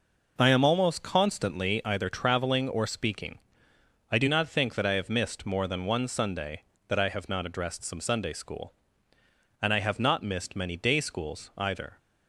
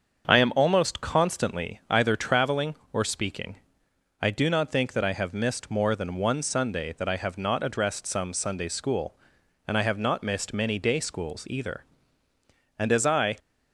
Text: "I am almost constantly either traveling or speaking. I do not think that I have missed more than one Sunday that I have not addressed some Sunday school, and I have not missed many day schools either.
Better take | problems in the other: first | starts louder than the rest; until 1.3 s; 7 dB // goes on to say "And as I"; from 12.7 s on; 0.58 s long

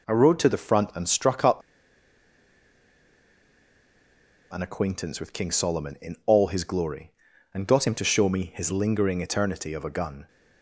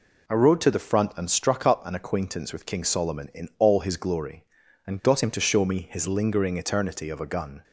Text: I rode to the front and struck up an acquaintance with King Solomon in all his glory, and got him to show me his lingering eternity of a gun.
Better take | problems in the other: second | pauses between "up" and "an"; strong; at 1.6 s; 2.9 s long

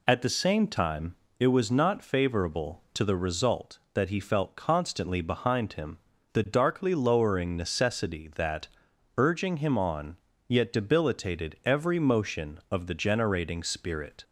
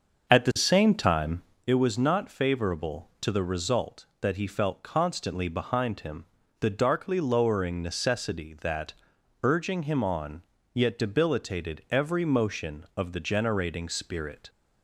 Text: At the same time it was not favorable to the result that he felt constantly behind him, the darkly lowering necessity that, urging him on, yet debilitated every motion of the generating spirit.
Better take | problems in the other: first | starts louder than the rest; until 1.7 s; 6.5 dB // pauses between "time" and "it"; slight; at 1.4 s; 0.24 s long; slight in the first

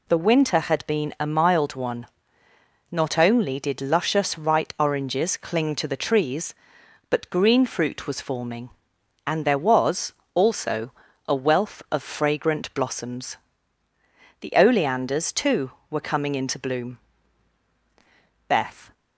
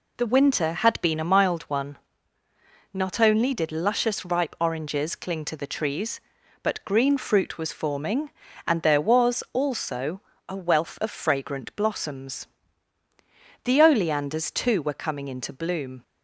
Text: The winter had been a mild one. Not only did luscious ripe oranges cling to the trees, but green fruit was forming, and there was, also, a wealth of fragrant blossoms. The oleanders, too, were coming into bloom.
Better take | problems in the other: second | goes on to say "Beth"; slight; from 18.4 s on; 0.44 s long

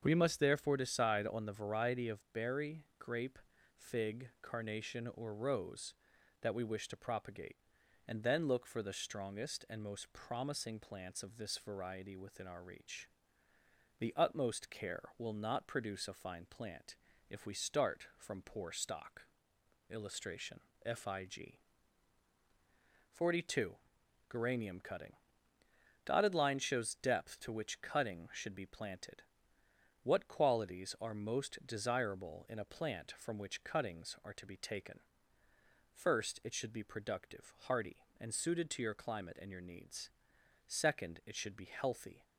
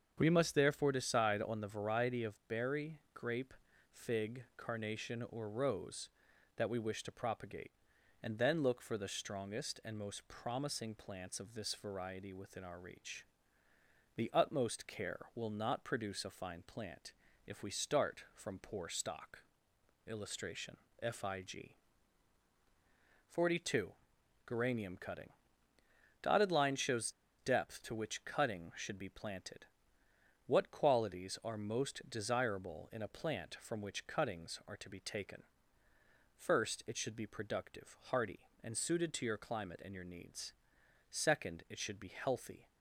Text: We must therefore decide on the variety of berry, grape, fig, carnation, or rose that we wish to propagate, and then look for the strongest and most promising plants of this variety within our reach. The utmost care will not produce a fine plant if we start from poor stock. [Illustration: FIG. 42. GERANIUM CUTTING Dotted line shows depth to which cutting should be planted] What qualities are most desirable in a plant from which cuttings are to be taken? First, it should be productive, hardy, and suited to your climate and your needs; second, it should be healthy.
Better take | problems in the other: first | starts louder than the rest; strong; until 1.1 s; 7 dB; strong in the first // pauses between "plant" and "if"; slight; at 17.1 s; 0.34 s long; slight in the first // pauses between "CUTTING" and "Dotted"; noticeable; at 25.2 s; 0.94 s long; noticeable in the first // pauses between "shows" and "depth"; slight; at 27.1 s; 0.28 s long // pauses between "planted" and "What"; noticeable; at 29.6 s; 0.80 s long; noticeable in the first

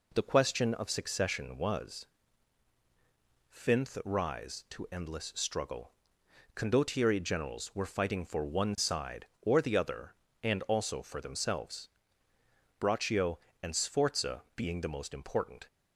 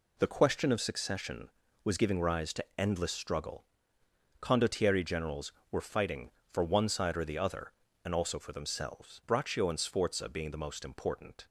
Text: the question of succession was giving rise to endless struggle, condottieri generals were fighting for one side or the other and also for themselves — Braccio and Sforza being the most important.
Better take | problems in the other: second | says "finth" for "giving"; at 3.4 s

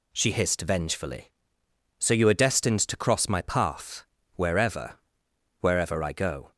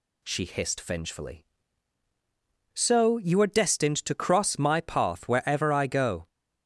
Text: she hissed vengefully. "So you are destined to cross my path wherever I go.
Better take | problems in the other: second | pauses between "path" and "wherever"; slight; at 4.0 s; 0.32 s long // says "wherever" twice; at 5.6 s

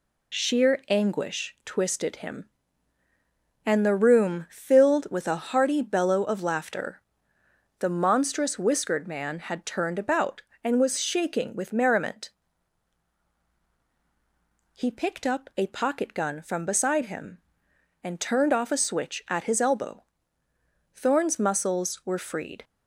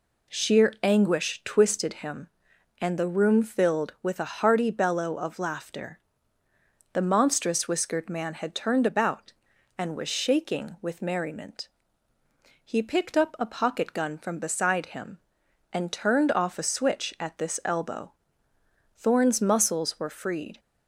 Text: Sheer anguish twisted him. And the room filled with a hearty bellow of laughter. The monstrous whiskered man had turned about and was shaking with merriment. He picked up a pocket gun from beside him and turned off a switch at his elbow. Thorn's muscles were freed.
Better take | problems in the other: first | says "this" for "his"; at 17.3 s

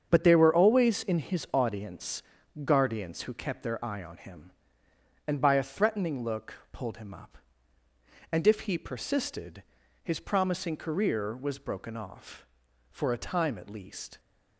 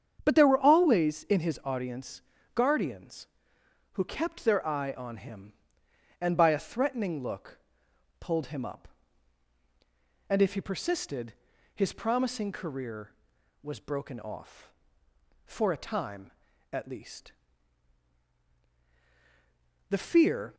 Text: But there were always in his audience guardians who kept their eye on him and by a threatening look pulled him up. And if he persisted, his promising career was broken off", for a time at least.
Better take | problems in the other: first | starts louder than the rest; strong; until 1.2 s; 8 dB; strong in the first // pauses between "audience" and "guardians"; slight; at 2.2 s; 0.34 s long; also in the first // pauses between "look" and "pulled"; noticeable; at 7.5 s; 0.62 s long; slight in the first // goes on to say "The fear"; noticeable; from 19.8 s on; 0.66 s long

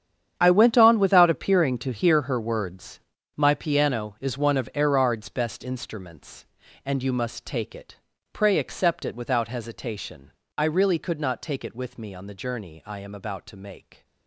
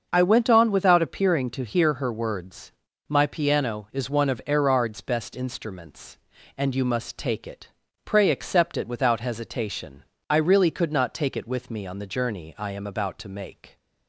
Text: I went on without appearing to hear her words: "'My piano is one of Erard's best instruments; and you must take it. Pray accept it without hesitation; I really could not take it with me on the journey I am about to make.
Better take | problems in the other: second | gets quieter; strong; throughout; 15 dB // starts louder than the rest; strong; until 1.3 s; 9 dB; also in the second

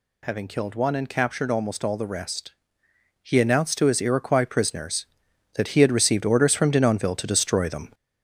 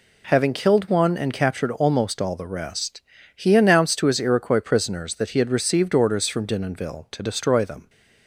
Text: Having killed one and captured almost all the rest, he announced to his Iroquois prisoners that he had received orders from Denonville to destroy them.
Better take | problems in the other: second | gets louder; noticeable; throughout; 4 dB

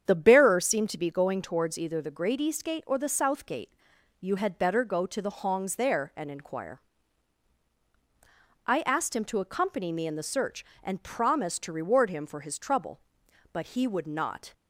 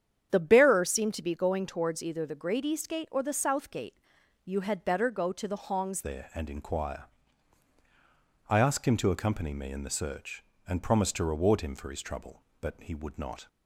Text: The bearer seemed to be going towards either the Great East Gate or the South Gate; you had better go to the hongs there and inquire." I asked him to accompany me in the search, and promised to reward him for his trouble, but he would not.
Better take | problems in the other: first | starts louder than the rest; strong; until 1.3 s; 8.5 dB; strong in the first // changes voice at "there"; from 6.0 s on; 7.4 s long

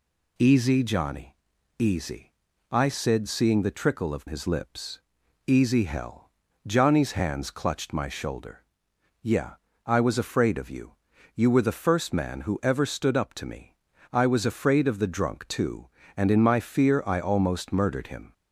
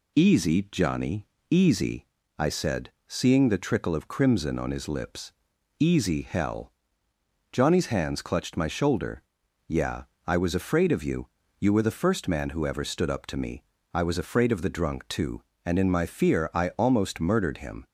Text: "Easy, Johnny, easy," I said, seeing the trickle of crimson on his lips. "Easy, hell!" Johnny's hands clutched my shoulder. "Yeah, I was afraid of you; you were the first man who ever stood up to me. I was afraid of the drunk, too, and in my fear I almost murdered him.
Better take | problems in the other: second | skips "crimson on"; at 4.2 s

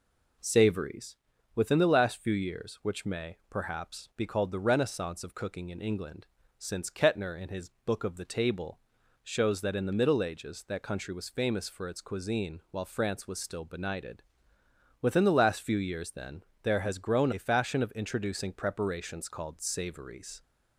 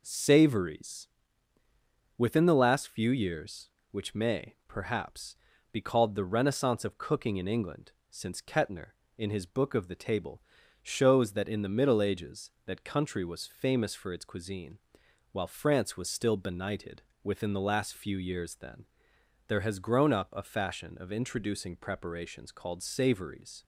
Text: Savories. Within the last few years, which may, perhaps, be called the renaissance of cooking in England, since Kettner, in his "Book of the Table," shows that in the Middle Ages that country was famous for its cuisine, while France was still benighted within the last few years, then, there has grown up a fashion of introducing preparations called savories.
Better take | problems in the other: second | pauses between "benighted" and "within"; noticeable; at 14.2 s; 0.78 s long; slight in the second // skips "up"; at 17.3 s

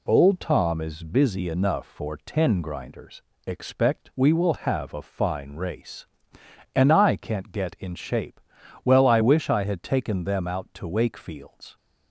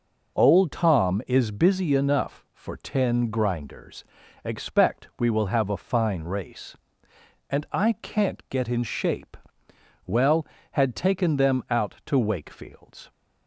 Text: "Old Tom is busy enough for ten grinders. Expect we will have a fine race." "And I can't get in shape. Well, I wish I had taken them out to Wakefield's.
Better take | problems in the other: first | skips "I wish I"; at 10.5 s

